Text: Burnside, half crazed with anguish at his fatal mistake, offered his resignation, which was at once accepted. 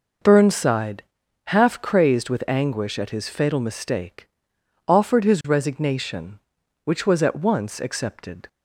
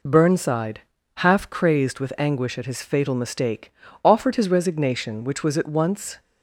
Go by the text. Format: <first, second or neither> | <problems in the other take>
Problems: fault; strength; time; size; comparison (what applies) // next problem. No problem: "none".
first | stops before "accepted"; at 6.1 s